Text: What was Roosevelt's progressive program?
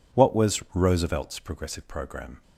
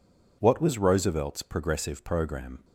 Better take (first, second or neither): neither